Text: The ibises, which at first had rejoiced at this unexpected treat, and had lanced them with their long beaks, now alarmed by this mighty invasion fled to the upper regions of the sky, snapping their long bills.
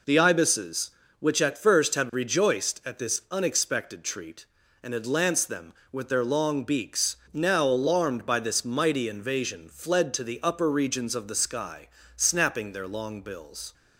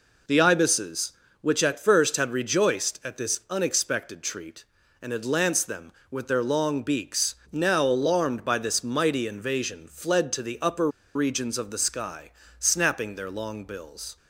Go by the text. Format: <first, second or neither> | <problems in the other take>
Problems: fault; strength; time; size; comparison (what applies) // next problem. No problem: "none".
first | pauses between "upper" and "regions"; slight; at 10.8 s; 0.25 s long